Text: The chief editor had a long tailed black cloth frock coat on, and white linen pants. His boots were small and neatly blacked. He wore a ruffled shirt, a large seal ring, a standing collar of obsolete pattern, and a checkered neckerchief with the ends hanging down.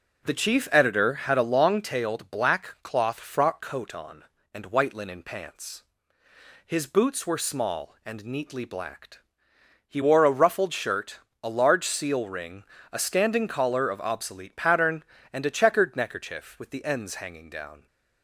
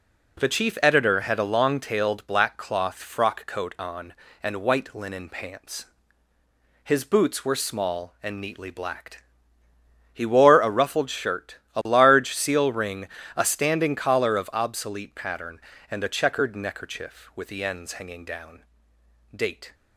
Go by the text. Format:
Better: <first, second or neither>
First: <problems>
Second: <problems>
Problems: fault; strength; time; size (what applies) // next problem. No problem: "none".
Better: first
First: none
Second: goes on to say "Date"; slight; from 19.3 s on; 0.38 s long